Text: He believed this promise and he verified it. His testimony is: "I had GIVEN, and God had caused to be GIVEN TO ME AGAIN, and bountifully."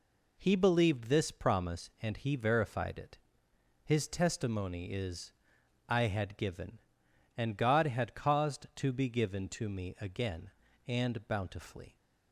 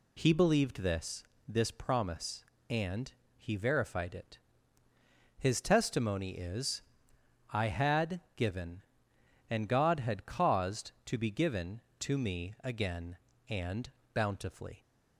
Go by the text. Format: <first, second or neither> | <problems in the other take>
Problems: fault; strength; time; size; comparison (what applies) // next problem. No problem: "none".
first | says "this" twice; at 1.4 s // pauses between "and" and "he"; slight; at 3.1 s; 0.26 s long // pauses between "had" and "GIVEN"; slight; at 8.1 s; 0.16 s long // pauses between "and" and "bountifully"; slight; at 13.8 s; 0.24 s long